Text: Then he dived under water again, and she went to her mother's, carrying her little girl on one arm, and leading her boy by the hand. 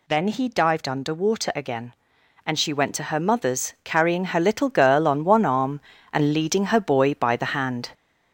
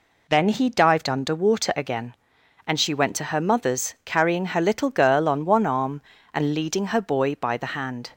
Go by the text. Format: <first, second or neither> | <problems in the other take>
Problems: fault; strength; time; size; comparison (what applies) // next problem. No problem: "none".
second | gets louder; noticeable; throughout; 4 dB